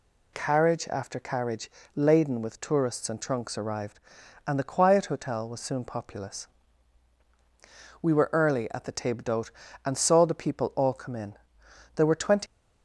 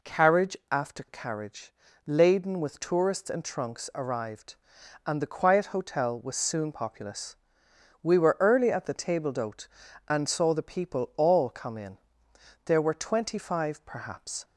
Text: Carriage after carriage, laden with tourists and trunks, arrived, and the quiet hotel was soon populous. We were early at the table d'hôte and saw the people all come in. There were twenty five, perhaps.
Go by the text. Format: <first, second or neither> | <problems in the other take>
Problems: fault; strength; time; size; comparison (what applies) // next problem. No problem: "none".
second | stops before "five perhaps"; at 12.4 s